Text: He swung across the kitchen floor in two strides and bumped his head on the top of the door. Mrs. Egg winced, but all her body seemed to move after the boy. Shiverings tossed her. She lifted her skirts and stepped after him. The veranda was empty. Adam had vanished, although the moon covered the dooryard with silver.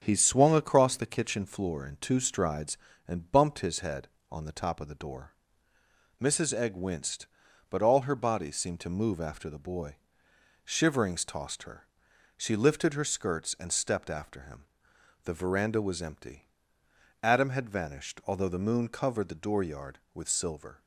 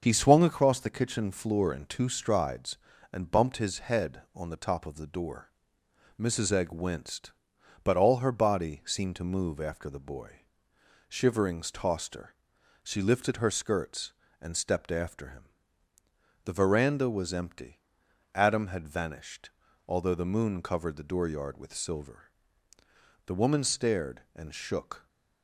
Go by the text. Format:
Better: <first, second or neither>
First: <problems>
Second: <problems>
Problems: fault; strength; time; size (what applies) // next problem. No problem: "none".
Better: first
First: starts louder than the rest; strong; until 1.0 s; 7.5 dB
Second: starts louder than the rest; until 1.0 s; 7 dB // goes on to say "The woman stared and shook"; strong; from 23.2 s on; 1.8 s long